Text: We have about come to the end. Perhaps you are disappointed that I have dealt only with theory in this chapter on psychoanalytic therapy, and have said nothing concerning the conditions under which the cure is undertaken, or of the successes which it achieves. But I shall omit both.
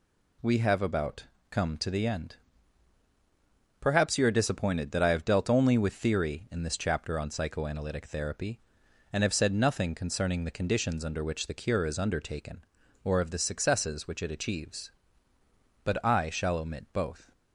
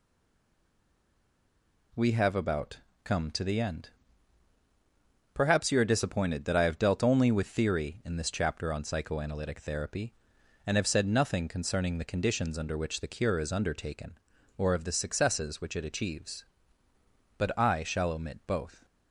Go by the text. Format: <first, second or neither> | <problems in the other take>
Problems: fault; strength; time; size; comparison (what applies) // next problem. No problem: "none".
first | stays silent before the first word; noticeable; until 1.9 s; 1.9 s long // pauses between "about" and "come"; slight; at 2.7 s; 0.26 s long; slight in the first